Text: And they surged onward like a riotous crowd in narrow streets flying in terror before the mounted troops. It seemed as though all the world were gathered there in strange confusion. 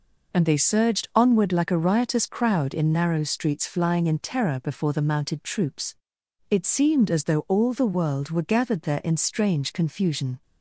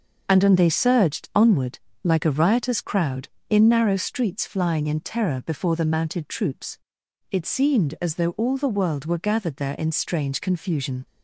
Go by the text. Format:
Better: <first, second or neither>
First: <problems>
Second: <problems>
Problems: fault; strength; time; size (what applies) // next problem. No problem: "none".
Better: first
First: none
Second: says "And" twice; at 0.4 s // pauses between "onward" and "like"; slight; at 1.7 s; 0.24 s long